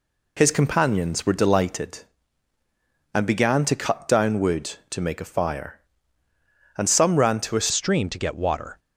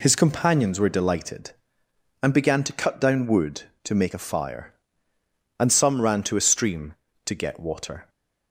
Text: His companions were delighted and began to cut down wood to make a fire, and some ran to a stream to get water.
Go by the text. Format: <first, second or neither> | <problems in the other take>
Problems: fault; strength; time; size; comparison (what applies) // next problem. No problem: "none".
second | changes voice at "stream"; from 7.7 s on; 1.0 s long